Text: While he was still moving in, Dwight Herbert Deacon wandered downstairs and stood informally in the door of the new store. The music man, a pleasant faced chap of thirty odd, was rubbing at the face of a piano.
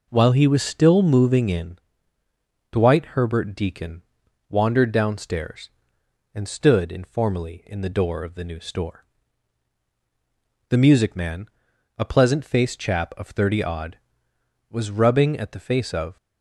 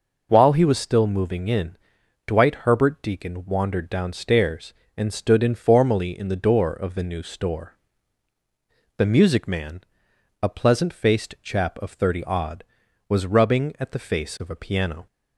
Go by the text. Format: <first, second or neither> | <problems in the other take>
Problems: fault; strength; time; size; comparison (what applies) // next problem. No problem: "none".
second | pauses between "Deacon" and "wandered"; noticeable; at 4.0 s; 0.46 s long // stops before "a piano"; at 16.1 s